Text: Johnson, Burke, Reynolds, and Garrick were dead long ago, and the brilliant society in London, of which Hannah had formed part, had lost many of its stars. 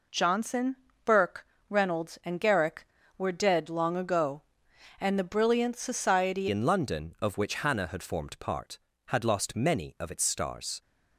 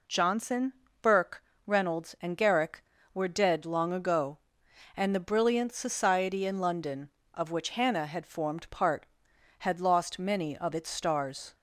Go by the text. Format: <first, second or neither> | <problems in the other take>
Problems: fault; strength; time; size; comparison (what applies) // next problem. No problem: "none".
second | changes voice at "in"; from 6.5 s on; 4.3 s long